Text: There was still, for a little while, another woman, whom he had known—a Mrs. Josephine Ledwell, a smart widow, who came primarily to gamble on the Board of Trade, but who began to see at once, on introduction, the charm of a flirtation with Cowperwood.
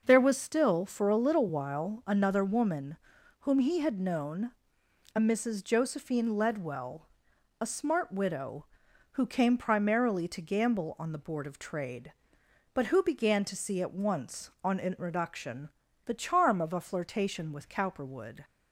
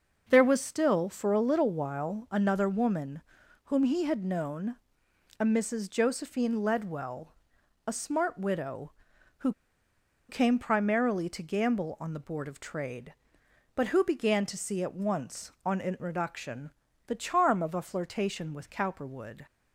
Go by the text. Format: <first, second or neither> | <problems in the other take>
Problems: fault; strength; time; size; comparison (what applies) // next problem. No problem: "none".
first | pauses between "who" and "came"; noticeable; at 9.5 s; 0.76 s long